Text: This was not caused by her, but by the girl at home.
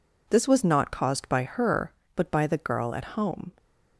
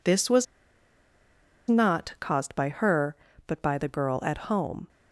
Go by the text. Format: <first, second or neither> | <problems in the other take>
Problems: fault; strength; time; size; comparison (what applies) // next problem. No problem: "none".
first | pauses between "was" and "not"; strong; at 0.4 s; 1.2 s long